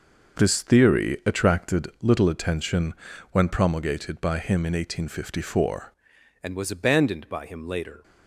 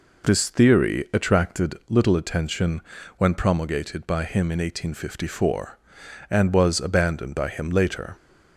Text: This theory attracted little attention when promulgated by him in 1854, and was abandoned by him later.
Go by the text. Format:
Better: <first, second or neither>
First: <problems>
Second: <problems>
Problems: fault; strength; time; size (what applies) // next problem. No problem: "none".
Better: second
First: pauses between "attention" and "when"; at 2.9 s; 0.38 s long // changes voice at "and"; from 6.4 s on; 1.6 s long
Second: pauses between "attention" and "when"; at 2.8 s; 0.37 s long